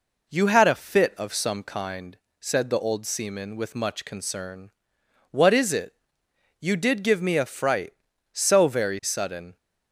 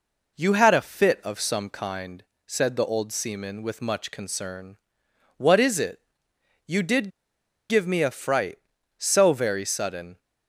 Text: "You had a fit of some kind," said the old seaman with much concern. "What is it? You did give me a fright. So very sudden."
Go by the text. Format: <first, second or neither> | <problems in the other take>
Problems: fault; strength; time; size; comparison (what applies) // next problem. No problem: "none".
first | pauses between "did" and "give"; noticeable; at 7.0 s; 0.60 s long